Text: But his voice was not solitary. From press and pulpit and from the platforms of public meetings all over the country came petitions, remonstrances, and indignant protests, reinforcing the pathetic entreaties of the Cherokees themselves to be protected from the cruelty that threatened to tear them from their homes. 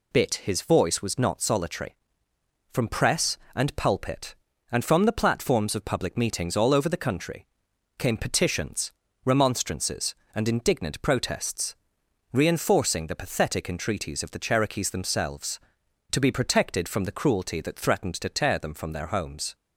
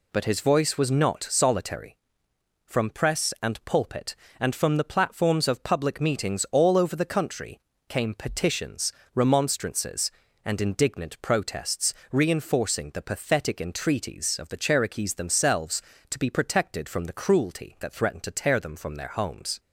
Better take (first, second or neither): second